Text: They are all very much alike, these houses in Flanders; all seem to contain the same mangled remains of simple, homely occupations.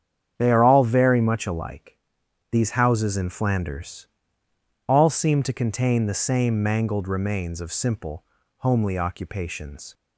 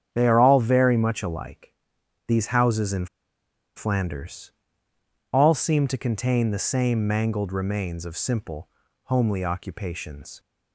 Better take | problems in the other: first | starts louder than the rest; strong; until 1.1 s; 8.5 dB; strong in the first // pauses between "in" and "Flanders"; noticeable; at 3.0 s; 0.70 s long

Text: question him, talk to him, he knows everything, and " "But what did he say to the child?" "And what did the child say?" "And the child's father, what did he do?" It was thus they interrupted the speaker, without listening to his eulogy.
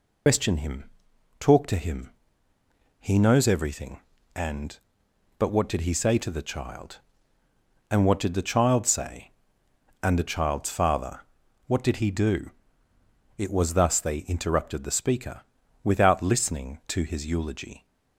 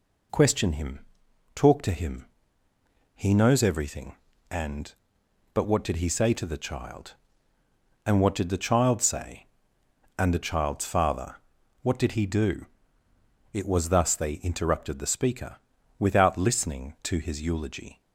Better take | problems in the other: second | loses the start of "question"; at 0.2 s; 105 ms

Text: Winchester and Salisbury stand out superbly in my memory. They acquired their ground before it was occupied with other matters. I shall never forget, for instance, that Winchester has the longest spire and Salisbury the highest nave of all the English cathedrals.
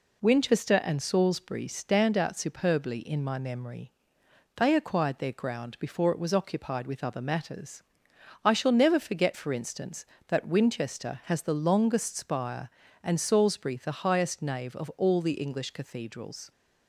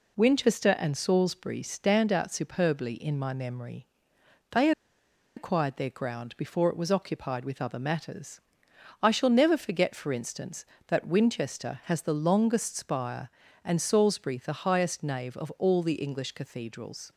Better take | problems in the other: first | pauses between "They" and "acquired"; noticeable; at 4.7 s; 0.65 s long

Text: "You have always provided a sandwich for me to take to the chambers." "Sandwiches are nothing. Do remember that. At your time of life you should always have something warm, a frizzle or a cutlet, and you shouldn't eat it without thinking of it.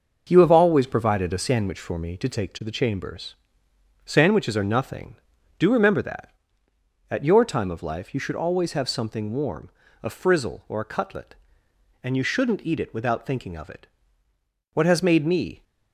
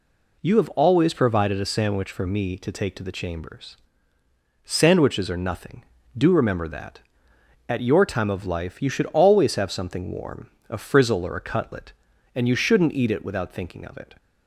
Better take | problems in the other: second | starts louder than the rest; noticeable; until 1.2 s; 6 dB // goes on to say "What has made me"; noticeable; from 14.7 s on; 0.88 s long

